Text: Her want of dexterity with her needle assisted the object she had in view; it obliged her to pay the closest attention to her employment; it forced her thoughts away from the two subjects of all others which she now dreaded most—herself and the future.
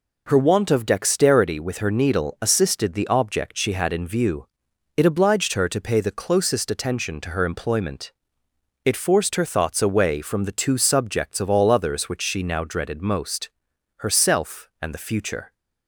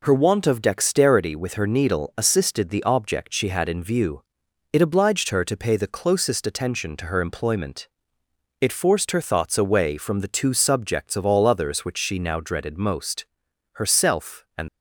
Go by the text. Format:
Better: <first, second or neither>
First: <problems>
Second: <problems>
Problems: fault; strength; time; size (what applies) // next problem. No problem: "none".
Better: first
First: none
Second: stops before "the future"; at 14.6 s